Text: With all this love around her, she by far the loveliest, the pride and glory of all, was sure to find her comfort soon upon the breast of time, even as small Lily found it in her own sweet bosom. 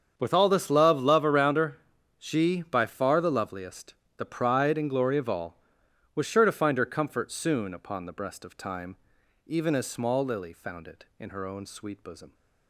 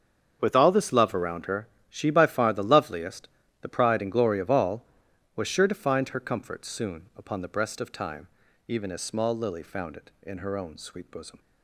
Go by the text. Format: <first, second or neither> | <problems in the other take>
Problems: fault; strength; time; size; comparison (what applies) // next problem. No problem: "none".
second | starts louder than the rest; strong; until 1.1 s; 7.5 dB; strong in the second // says "love" twice; at 1.0 s